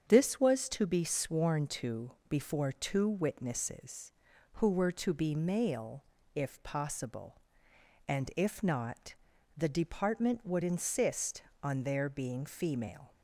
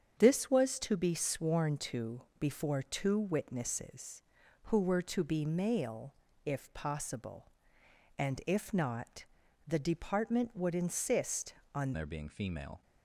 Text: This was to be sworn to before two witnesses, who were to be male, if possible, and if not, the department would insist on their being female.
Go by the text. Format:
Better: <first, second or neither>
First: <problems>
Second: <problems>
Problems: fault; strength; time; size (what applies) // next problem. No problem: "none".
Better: first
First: starts louder than the rest; strong; until 1.0 s; 7.5 dB // pauses between "to" and "before"; slight; at 2.1 s; 0.18 s long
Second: starts louder than the rest; strong; until 1.1 s; 7.5 dB // pauses between "to" and "before"; slight; at 2.2 s; 0.18 s long // changes voice at "their"; from 11.9 s on; 0.9 s long